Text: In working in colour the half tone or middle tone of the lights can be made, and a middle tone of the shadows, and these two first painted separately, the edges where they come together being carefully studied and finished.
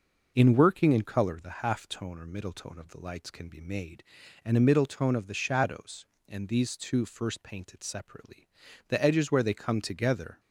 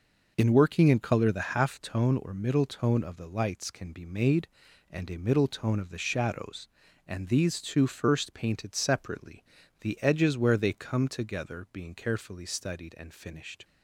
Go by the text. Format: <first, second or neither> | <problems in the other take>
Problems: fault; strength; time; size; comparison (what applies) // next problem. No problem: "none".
second | stops before "being carefully studied and finished"; at 10.3 s